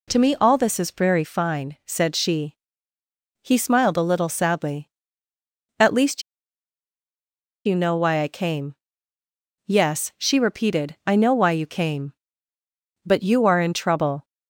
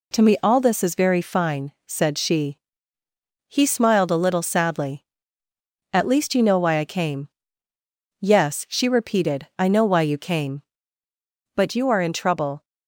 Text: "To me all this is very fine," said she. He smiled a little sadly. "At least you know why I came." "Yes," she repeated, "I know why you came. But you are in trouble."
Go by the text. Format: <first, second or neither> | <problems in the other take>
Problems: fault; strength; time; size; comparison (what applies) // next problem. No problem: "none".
second | pauses between "least" and "you"; strong; at 6.2 s; 1.4 s long